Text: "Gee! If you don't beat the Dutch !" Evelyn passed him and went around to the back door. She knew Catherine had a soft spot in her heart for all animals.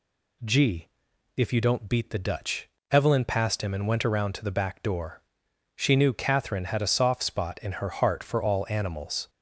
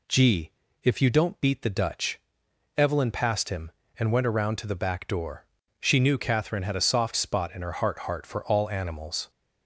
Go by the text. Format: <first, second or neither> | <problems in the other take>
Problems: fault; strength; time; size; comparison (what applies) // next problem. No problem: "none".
first | says "heart" twice; at 8.0 s